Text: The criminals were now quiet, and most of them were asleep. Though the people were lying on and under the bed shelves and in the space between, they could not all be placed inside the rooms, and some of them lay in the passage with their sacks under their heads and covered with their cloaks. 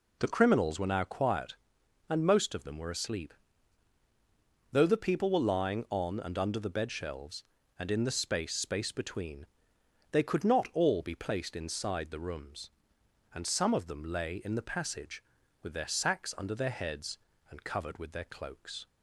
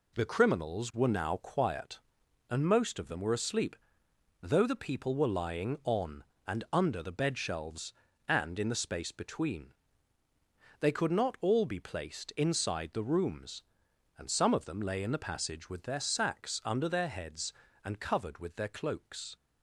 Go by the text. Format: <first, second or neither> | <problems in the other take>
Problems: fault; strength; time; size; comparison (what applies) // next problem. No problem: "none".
second | says "space" twice; at 8.5 s